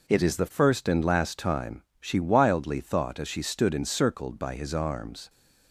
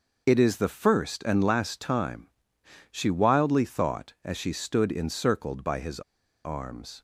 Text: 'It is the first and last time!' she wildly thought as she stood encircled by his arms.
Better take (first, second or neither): first